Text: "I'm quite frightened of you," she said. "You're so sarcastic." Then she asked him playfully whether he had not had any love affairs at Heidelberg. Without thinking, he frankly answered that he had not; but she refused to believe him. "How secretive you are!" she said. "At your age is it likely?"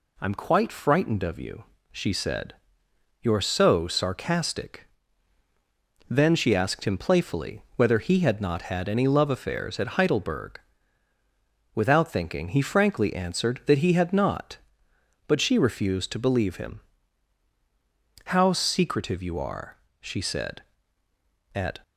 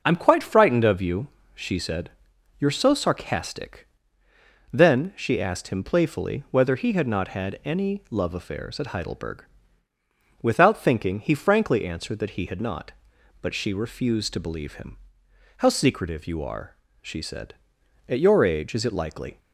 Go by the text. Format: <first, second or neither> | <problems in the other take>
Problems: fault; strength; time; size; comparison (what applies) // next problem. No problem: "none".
second | stops before "your age is it likely"; at 21.8 s